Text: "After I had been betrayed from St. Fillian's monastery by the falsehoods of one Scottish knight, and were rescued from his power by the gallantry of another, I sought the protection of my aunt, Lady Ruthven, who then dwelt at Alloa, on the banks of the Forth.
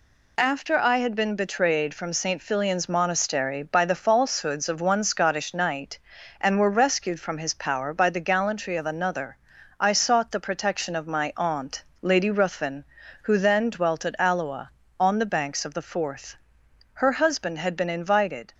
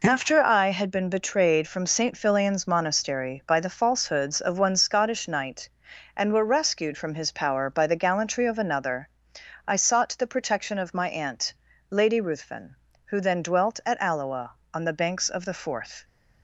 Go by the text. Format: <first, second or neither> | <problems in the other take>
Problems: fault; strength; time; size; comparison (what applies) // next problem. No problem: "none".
second | goes on to say "Her husband had been invited"; from 16.9 s on; 1.6 s long